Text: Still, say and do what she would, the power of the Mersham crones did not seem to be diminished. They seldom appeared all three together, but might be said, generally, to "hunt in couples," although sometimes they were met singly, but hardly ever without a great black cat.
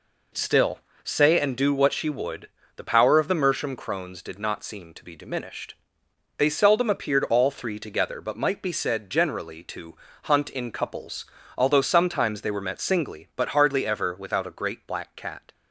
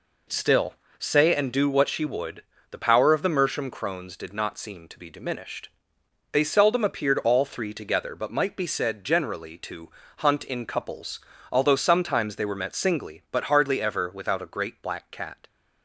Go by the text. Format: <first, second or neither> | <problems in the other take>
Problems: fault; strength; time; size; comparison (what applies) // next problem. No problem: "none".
neither | pauses between "to" and "hunt"; slight; the same in both